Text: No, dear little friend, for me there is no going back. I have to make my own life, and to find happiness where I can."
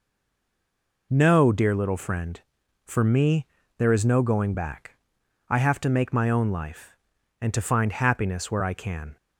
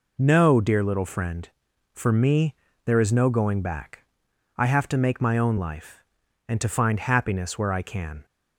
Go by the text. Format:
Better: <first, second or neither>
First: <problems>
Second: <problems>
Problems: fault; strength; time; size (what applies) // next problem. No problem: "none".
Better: second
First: stays silent before the first word; until 1.1 s; 1.1 s long // pauses between "me" and "there"; slight; at 3.4 s; 0.32 s long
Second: pauses between "me" and "there"; slight; at 2.5 s; 0.31 s long